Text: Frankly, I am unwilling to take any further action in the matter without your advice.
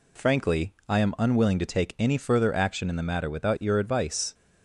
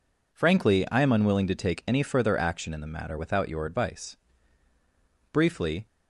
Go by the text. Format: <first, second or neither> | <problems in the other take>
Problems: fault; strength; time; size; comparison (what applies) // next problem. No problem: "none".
first | goes on to say "Briefly"; from 5.3 s on; 0.54 s long